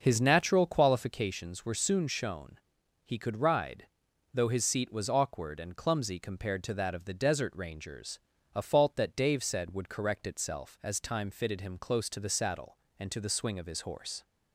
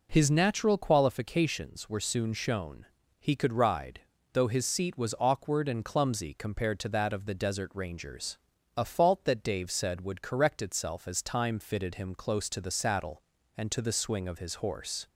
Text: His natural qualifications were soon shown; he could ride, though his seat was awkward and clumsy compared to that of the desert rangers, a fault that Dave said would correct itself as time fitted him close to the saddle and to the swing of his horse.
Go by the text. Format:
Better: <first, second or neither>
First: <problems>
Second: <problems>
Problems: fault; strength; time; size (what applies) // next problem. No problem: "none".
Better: second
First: starts louder than the rest; noticeable; until 1.3 s; 6 dB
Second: none